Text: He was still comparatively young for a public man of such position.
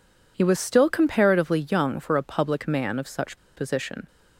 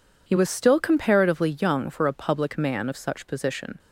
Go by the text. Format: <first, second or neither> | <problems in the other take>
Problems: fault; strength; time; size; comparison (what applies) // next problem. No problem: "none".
second | pauses between "such" and "position"; slight; at 3.3 s; 0.18 s long